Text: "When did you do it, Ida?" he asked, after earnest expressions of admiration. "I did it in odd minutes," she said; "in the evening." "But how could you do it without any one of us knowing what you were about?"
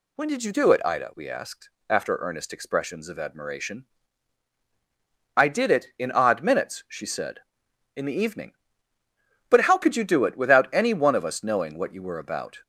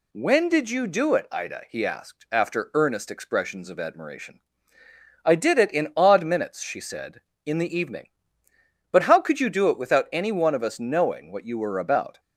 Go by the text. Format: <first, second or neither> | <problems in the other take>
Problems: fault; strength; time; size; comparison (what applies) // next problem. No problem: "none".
second | says "we" for "he"; at 1.1 s